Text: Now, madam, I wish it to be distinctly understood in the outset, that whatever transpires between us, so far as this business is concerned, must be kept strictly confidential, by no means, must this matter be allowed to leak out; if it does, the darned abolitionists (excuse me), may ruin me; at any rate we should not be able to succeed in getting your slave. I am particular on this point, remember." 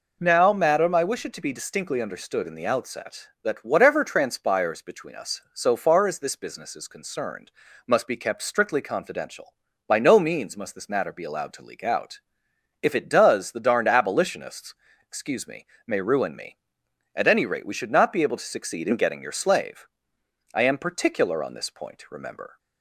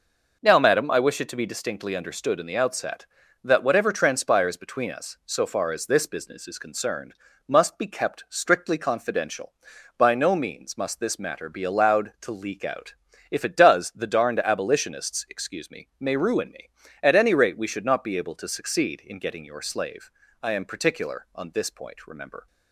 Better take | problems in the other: neither | none

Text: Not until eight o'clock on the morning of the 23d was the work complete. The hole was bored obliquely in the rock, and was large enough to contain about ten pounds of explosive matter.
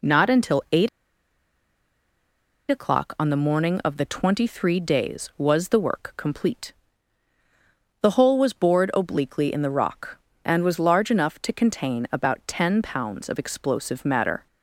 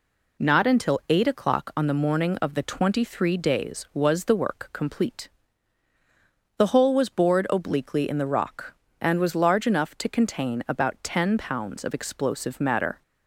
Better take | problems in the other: second | pauses between "eight" and "o'clock"; strong; at 0.8 s; 1.8 s long

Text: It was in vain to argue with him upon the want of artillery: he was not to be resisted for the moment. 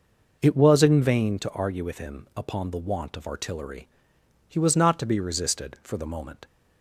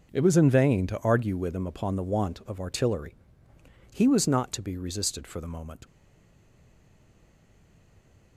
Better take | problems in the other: first | stays silent after the last word; from 5.8 s on; 2.5 s long

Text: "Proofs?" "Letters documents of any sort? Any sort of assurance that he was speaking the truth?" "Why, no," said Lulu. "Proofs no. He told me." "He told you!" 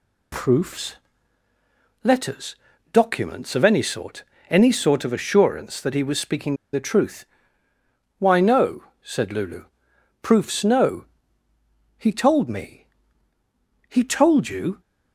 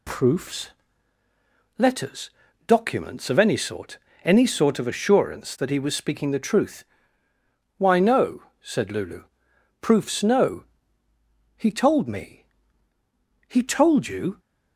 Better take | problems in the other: second | pauses between "Letters" and "documents"; slight; at 2.5 s; 0.36 s long; slight in the second // pauses between "speaking" and "the"; slight; at 6.5 s; 0.18 s long

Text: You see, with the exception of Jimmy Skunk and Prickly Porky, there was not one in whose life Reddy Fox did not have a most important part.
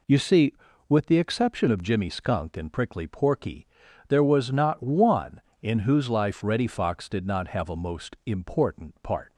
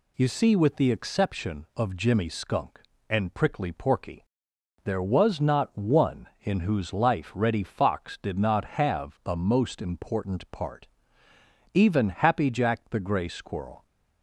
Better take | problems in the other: first | goes on to say "Even Happy Jack the Gray Squirrel"; strong; from 11.7 s on; 2.1 s long

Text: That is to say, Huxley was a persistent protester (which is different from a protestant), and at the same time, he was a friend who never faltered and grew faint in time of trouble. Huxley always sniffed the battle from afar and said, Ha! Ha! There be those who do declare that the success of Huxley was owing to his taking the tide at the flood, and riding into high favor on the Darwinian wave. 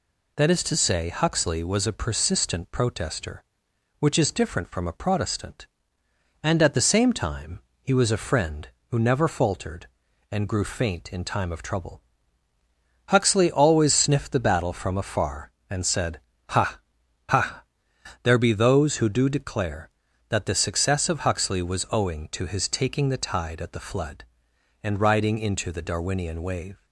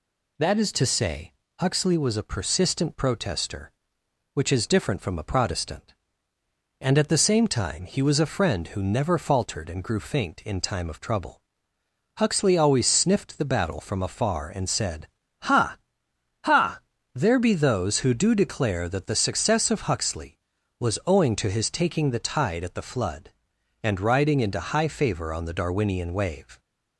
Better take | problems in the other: second | skips "high favor on"; at 25.7 s

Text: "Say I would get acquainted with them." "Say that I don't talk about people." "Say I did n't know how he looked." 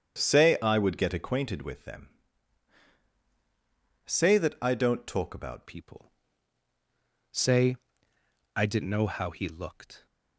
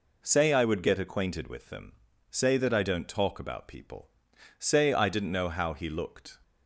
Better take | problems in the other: second | starts louder than the rest; strong; until 1.2 s; 8 dB // changes voice at "people"; from 5.6 s on; 4.4 s long // pauses between "Say" and "I"; noticeable; at 7.7 s; 0.78 s long

